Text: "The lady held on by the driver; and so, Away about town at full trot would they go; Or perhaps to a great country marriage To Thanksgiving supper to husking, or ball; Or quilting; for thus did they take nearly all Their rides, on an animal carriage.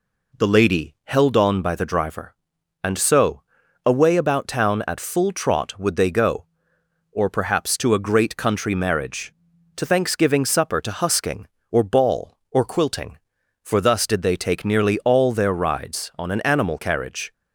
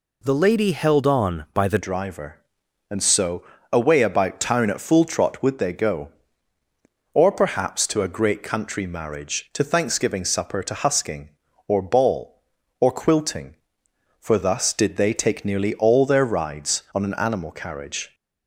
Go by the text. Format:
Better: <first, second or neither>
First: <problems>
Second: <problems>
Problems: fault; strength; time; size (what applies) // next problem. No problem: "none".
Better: first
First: none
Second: changes voice at "driver"; from 1.8 s on; 16.3 s long